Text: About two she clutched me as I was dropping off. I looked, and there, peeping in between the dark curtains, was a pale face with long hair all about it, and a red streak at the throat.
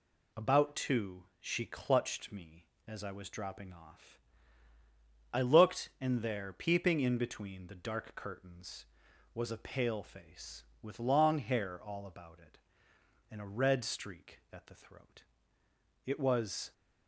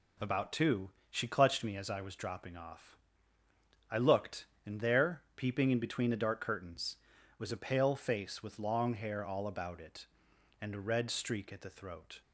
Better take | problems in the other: second | pauses between "two" and "she"; slight; at 1.2 s; 0.16 s long; slight in the second // goes on to say "It was"; noticeable; from 16.0 s on; 0.68 s long

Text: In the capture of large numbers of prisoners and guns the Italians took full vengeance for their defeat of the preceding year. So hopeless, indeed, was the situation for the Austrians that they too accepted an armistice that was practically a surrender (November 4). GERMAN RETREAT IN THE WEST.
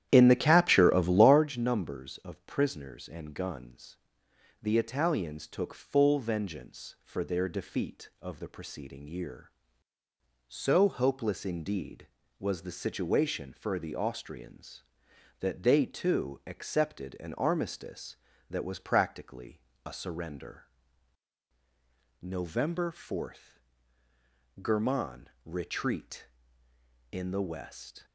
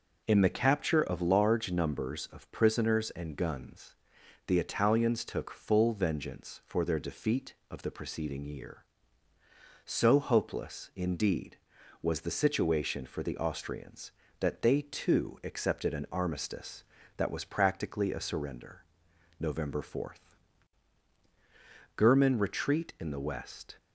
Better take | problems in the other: second | starts louder than the rest; strong; until 1.5 s; 11.5 dB // pauses between "guns" and "the"; noticeable; at 3.9 s; 0.64 s long; noticeable in the second // pauses between "practically" and "a"; slight; at 19.6 s; 0.24 s long // pauses between "GERMAN" and "RETREAT"; slight; at 25.2 s; 0.16 s long

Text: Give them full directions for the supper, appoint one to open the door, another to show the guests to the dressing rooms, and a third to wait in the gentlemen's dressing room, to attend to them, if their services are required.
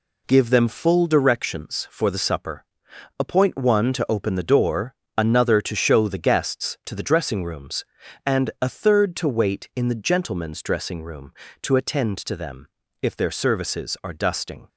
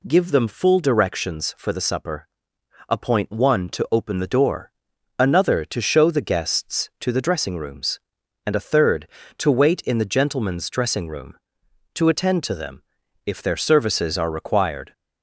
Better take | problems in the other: second | says "dusting" for "required"; at 14.1 s

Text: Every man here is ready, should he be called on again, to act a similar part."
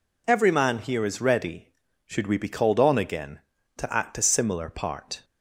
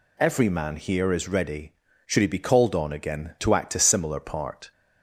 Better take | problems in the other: second | says "we" for "he"; at 2.2 s

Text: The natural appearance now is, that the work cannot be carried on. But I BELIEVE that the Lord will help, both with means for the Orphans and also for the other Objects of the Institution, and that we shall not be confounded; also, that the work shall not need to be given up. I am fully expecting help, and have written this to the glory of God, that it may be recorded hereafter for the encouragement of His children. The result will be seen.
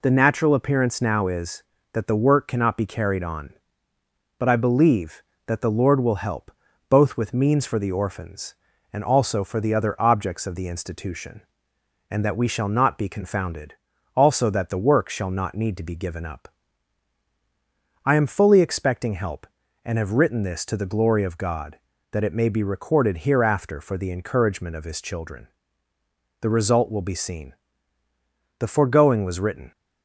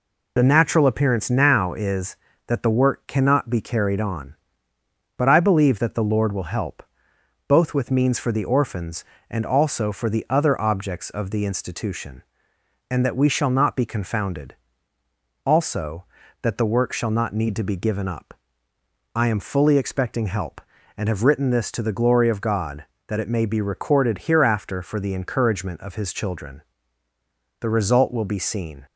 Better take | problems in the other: second | goes on to say "The foregoing was written"; noticeable; from 28.5 s on; 1.1 s long

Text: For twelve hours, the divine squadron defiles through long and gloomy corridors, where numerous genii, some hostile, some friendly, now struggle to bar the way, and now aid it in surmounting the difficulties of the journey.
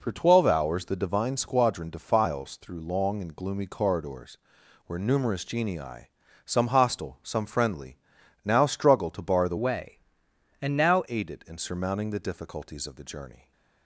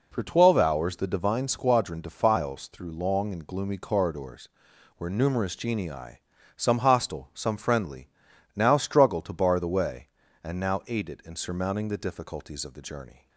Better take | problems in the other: second | changes voice from "way" to "now"; from 9.5 to 11.0 s; 1.5 s long

